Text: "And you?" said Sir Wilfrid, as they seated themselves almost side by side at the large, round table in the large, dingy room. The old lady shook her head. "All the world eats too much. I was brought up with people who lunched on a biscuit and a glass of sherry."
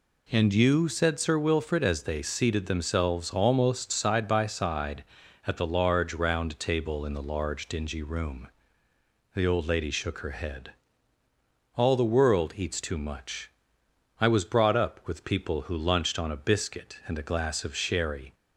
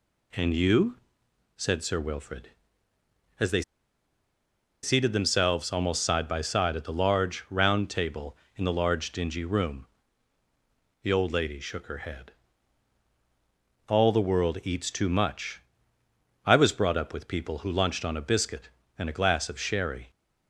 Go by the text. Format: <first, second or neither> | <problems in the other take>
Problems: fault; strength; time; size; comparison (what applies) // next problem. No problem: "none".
first | pauses between "they" and "seated"; at 3.6 s; 1.2 s long